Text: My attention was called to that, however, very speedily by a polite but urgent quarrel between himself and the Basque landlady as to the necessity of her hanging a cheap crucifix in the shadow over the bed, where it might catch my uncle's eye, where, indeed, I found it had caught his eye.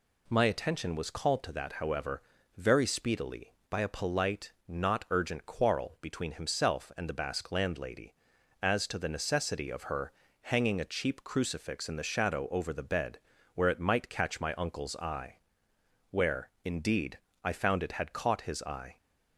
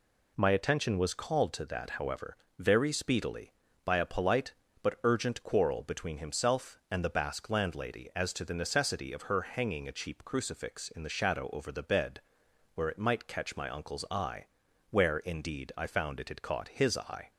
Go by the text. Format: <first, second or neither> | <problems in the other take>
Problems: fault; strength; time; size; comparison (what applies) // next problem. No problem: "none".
second | says "not" for "but"; at 4.6 s // pauses between "her" and "hanging"; slight; at 10.1 s; 0.32 s long